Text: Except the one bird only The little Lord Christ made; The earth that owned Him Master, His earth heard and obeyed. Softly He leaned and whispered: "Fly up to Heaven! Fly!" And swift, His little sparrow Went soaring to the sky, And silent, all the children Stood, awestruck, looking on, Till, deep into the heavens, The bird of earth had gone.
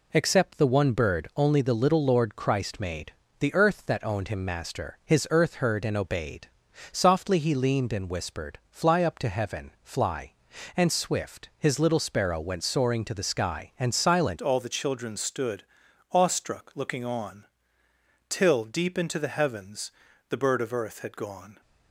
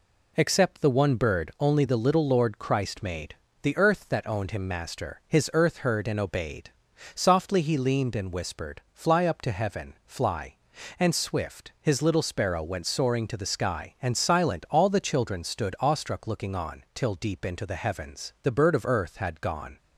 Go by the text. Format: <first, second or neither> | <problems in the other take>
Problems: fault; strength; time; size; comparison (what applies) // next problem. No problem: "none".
second | changes voice at "all"; from 14.4 s on; 7.2 s long